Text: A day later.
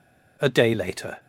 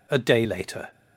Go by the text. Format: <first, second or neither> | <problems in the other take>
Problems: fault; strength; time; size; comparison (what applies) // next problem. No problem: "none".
neither | none